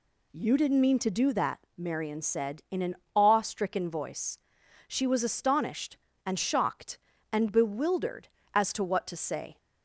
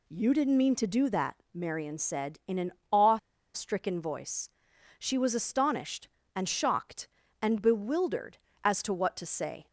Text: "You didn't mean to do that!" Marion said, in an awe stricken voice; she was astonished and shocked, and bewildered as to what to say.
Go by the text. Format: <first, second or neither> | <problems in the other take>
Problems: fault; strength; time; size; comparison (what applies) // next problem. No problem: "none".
first | pauses between "an" and "awe"; slight; at 2.7 s; 0.20 s long; slight in the first // pauses between "awe" and "stricken"; at 3.1 s; 0.36 s long